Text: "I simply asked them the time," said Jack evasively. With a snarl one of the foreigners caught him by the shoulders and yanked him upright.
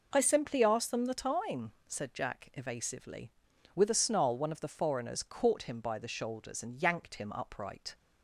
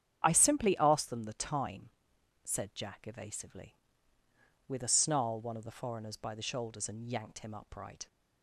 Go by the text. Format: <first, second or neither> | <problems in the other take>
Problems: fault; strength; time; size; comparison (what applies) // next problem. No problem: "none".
first | starts louder than the rest; strong; until 1.2 s; 8.5 dB // skips "caught him"; at 6.1 s